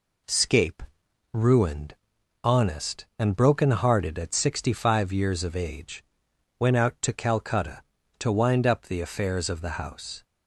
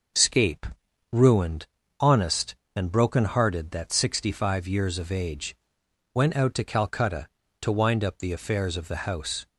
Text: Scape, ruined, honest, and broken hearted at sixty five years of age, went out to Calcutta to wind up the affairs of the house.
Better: first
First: none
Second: says "that" for "at"; at 3.7 s

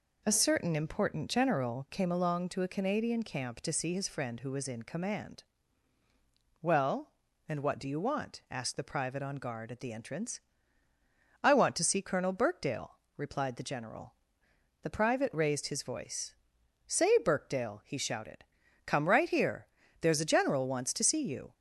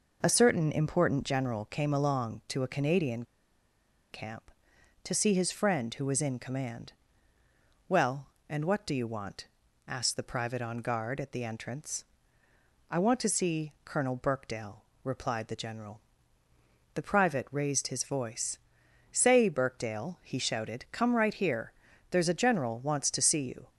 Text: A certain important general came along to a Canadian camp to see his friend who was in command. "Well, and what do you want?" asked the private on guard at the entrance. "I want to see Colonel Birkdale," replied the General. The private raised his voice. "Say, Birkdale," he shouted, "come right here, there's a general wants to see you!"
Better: first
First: none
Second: pauses between "Canadian" and "camp"; noticeable; at 3.2 s; 0.88 s long

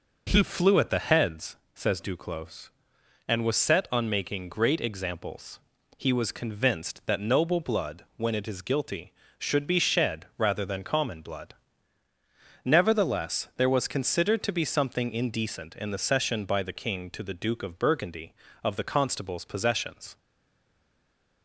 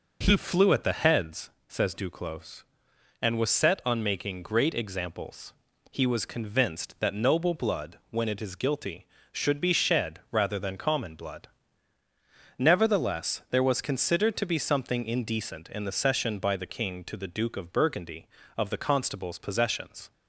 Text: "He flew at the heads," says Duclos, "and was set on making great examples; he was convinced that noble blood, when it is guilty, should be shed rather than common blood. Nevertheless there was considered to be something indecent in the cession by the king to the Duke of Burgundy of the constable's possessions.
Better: second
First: stays silent after the last word; noticeable; from 20.1 s on; 1.3 s long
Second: none

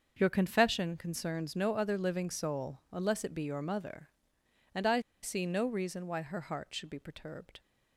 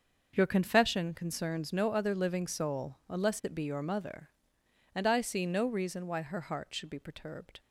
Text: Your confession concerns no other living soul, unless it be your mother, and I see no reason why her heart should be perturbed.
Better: second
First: starts louder than the rest; until 1.1 s; 6.5 dB // pauses between "I" and "see"; slight; at 4.9 s; 0.23 s long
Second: starts louder than the rest; until 1.3 s; 6.5 dB

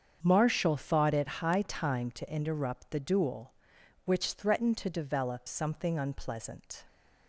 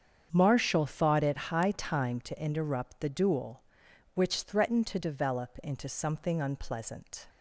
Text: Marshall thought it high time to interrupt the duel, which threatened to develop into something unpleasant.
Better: second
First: starts louder than the rest; strong; until 1.2 s; 7.5 dB // skips "into"; at 5.4 s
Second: starts louder than the rest; strong; until 1.3 s; 7.5 dB

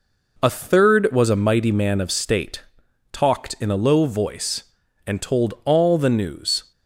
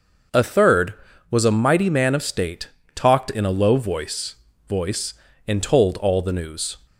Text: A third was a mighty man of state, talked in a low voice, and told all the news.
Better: first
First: none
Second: starts louder than the rest; until 1.7 s; 6 dB // says "voice" twice; at 4.6 s

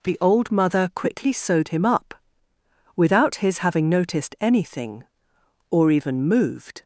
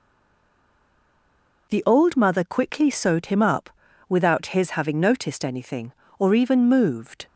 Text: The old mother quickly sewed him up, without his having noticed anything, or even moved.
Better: first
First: none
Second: stays silent before the first word; noticeable; until 1.6 s; 1.6 s long

